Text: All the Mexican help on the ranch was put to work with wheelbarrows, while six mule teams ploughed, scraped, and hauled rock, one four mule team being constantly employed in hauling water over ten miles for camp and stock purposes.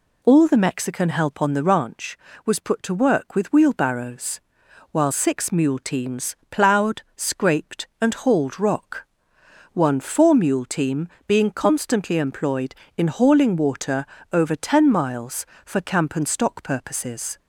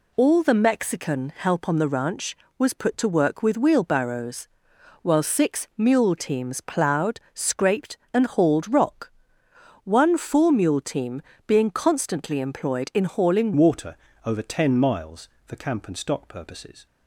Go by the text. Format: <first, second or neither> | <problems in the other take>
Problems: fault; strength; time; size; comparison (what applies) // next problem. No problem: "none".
first | pauses between "team" and "being"; slight; at 11.2 s; 0.24 s long; slight in the first // changes voice at "water"; from 13.5 s on; 3.3 s long // pauses between "water" and "over"; slight; at 13.9 s; 0.28 s long; slight in the first